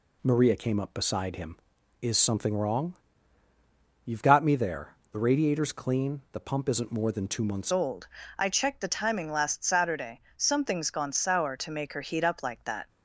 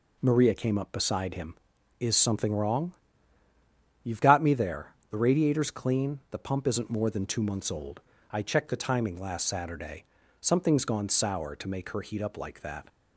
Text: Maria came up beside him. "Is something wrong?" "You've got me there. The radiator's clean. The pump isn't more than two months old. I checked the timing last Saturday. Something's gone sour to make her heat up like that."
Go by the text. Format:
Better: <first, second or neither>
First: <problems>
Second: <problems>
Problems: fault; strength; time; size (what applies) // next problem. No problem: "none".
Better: second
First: changes voice at "old"; from 7.7 s on; 5.1 s long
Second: none